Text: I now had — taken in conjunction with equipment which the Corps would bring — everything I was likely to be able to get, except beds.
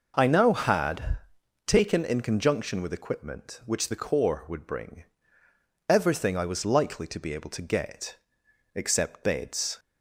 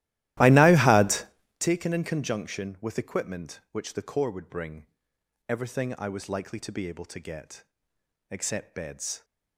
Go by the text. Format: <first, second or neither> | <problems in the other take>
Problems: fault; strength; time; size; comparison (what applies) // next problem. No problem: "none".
first | starts louder than the rest; strong; until 1.6 s; 15 dB